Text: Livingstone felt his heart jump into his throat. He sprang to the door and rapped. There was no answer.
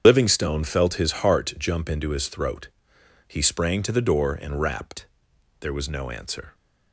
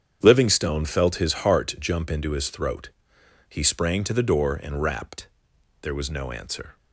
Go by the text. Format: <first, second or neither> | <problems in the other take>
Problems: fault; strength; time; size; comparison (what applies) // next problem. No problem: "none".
second | loses the start of "Livingstone"; at 0.0 s; 35 ms // starts louder than the rest; strong; until 1.0 s; 8 dB; strong in the second